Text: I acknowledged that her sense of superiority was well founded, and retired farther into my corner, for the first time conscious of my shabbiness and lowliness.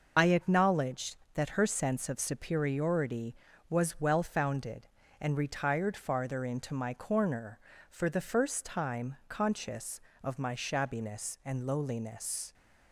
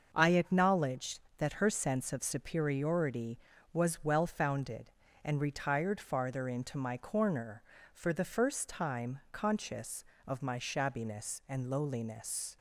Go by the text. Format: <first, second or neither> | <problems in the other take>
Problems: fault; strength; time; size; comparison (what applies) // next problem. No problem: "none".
second | loses the start of "I"; at 0.1 s; 65 ms // starts louder than the rest; noticeable; until 1.1 s; 6 dB; also in the second